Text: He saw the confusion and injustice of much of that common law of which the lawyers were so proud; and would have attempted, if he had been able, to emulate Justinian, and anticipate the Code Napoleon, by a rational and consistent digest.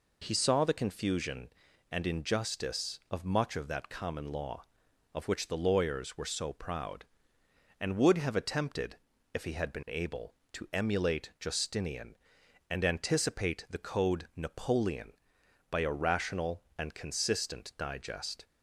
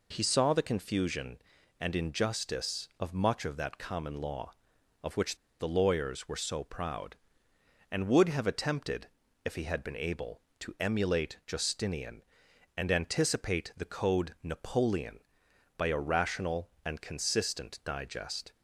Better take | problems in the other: first | pauses between "which" and "the"; slight; at 5.3 s; 0.22 s long

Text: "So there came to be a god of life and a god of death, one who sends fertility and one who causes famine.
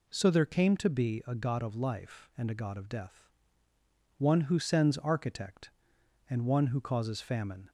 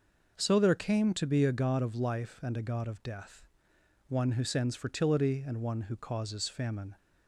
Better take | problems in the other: second | says "architect" for "fertility"; at 4.9 s

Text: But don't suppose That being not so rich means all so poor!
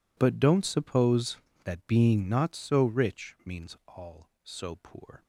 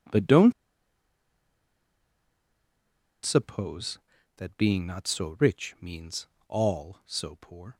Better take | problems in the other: first | pauses between "don't" and "suppose"; strong; at 0.5 s; 2.7 s long // pauses between "means" and "all"; slight; at 6.2 s; 0.20 s long

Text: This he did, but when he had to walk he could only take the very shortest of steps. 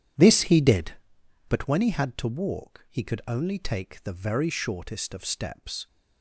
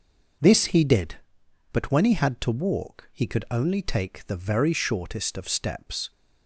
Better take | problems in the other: second | starts louder than the rest; strong; until 1.6 s; 9.5 dB

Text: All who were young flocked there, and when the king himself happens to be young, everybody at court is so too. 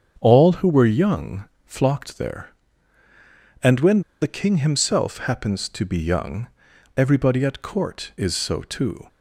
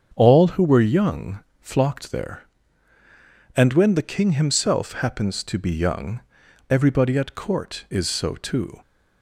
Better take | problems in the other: second | starts louder than the rest; strong; until 1.2 s; 7 dB; strong in the second // pauses between "young" and "flocked"; slight; at 1.4 s; 0.20 s long; slight in the second // pauses between "when" and "the"; slight; at 4.0 s; 0.20 s long

